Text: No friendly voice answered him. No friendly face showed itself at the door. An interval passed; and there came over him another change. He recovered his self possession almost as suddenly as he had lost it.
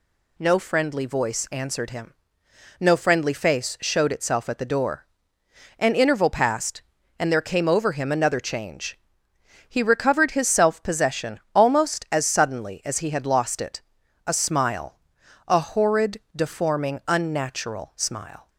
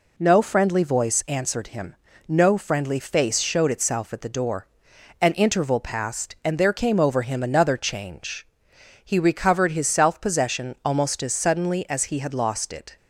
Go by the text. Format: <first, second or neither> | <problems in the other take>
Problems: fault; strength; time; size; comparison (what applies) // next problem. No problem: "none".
second | pauses between "possession" and "almost"; slight; at 11.3 s; 0.16 s long // goes on to say "A smile a horrid deforming unnatural smile"; strong; from 14.2 s on; 4.2 s long